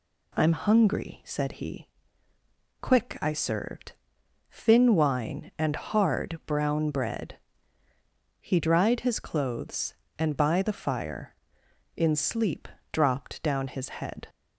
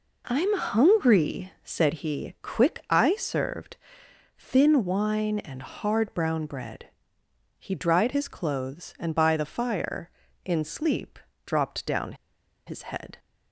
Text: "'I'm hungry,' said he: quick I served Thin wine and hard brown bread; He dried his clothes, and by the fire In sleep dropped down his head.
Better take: first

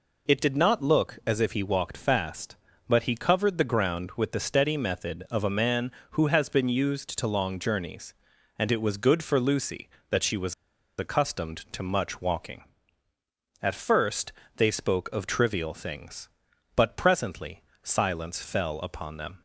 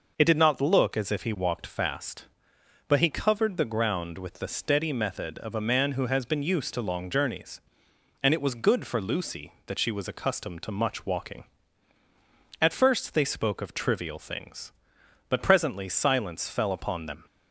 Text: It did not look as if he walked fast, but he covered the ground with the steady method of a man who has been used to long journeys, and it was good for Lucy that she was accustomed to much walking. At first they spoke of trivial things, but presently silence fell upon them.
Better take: second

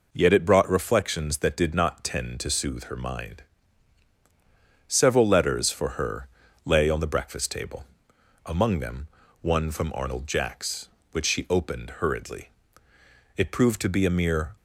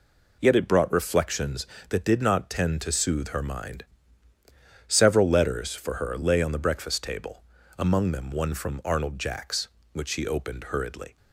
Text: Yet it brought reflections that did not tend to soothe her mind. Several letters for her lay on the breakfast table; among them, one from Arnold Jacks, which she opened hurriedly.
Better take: second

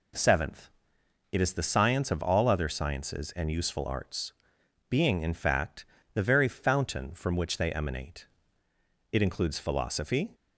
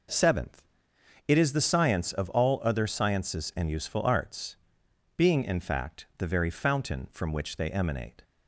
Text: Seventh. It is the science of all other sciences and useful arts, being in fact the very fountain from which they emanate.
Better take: second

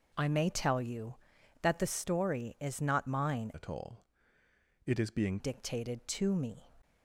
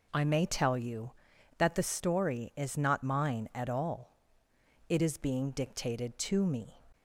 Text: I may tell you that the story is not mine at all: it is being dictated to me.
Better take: second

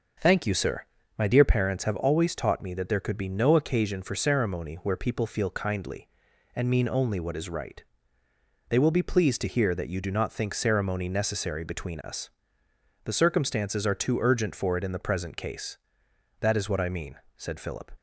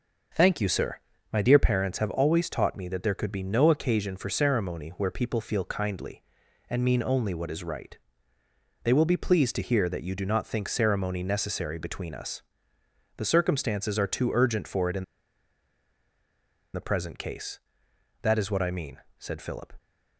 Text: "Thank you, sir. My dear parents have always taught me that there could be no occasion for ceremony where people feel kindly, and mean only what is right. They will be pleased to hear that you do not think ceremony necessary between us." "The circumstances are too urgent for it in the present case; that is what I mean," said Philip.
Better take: first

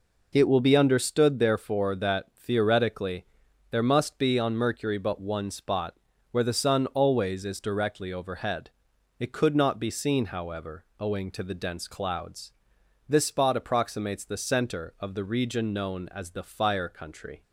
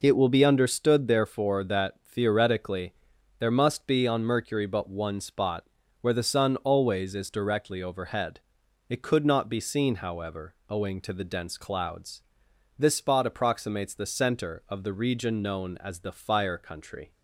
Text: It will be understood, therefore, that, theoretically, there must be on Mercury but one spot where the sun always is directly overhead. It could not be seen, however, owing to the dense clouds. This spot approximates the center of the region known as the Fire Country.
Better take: neither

